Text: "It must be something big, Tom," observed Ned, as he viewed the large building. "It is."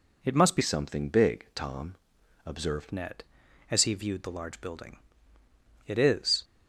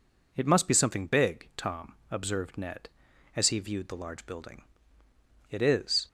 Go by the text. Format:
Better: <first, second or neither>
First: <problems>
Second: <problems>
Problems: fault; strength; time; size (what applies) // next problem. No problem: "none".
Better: second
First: changes voice from "something" to "observed"; from 0.6 to 2.9 s; 2.3 s long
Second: none